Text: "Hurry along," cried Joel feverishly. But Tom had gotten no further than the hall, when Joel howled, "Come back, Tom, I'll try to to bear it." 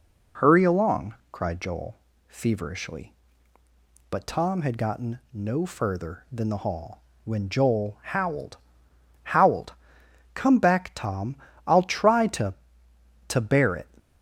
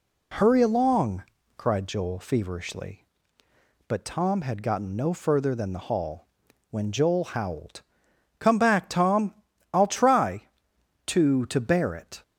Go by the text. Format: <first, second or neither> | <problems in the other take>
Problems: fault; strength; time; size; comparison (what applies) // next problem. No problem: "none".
second | pauses between "Joel" and "feverishly"; slight; at 1.9 s; 0.32 s long // says "howled" twice; at 9.3 s